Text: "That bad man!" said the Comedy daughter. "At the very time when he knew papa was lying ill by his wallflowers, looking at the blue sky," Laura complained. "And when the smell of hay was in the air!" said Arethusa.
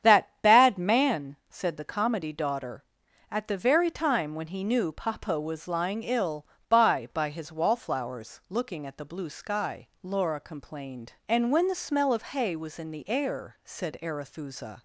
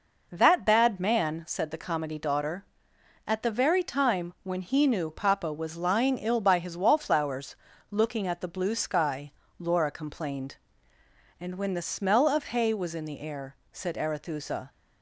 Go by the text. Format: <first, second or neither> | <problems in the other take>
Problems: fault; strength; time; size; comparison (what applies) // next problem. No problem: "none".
second | starts louder than the rest; strong; until 1.1 s; 8.5 dB // says "by" twice; at 7.1 s